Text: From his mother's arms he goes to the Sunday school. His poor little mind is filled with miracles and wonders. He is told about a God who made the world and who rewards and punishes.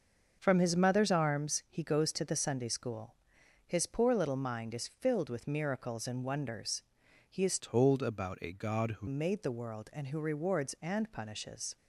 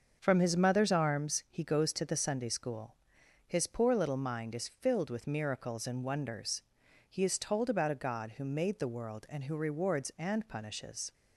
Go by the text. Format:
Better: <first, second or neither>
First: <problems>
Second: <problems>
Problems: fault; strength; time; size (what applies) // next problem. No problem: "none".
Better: second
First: starts louder than the rest; noticeable; until 1.4 s; 6 dB // changes voice from "told" to "who"; from 7.5 to 9.0 s; 1.5 s long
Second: starts louder than the rest; until 1.2 s; 6.5 dB